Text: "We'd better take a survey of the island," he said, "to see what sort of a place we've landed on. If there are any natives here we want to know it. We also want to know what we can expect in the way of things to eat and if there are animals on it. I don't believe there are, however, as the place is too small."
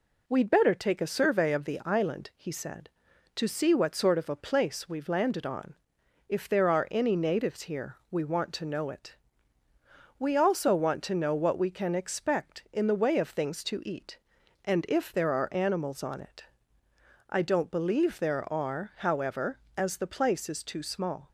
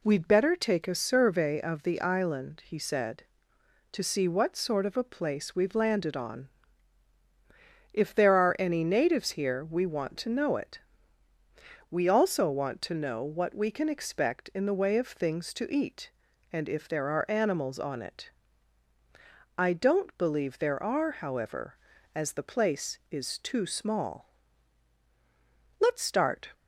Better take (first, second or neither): first